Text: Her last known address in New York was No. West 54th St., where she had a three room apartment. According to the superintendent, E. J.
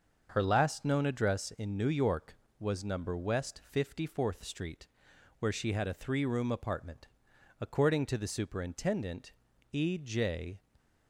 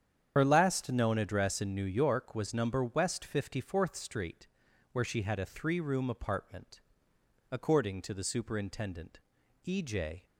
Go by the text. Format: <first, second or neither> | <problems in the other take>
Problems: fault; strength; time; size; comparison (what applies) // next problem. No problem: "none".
first | loses the start of "Her"; at 0.3 s; 70 ms // starts louder than the rest; strong; until 1.3 s; 8.5 dB; also in the first